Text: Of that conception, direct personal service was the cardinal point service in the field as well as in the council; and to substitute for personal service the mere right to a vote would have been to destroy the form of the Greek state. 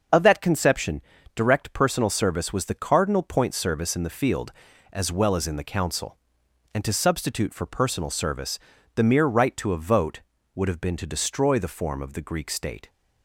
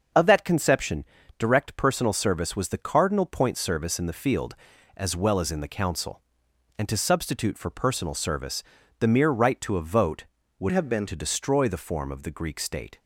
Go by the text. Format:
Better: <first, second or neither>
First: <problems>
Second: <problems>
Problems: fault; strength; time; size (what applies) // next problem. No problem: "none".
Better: first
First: starts louder than the rest; until 1.4 s; 6.5 dB // pauses between "service" and "the"; slight; at 8.5 s; 0.36 s long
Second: starts louder than the rest; until 1.4 s; 6.5 dB // pauses between "service" and "the"; slight; at 8.6 s; 0.36 s long // changes voice from "have" to "been"; from 10.7 to 11.0 s; 0.3 s long